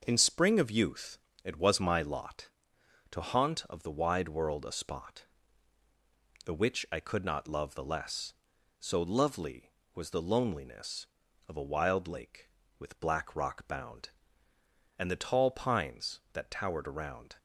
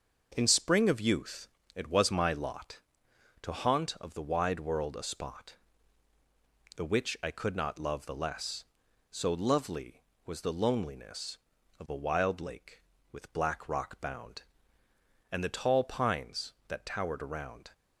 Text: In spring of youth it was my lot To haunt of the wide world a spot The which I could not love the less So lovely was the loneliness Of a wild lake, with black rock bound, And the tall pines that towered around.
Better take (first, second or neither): neither